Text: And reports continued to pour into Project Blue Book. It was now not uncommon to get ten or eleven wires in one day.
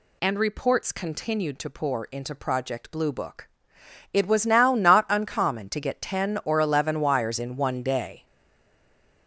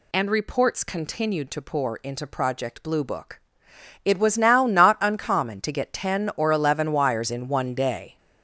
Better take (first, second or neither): second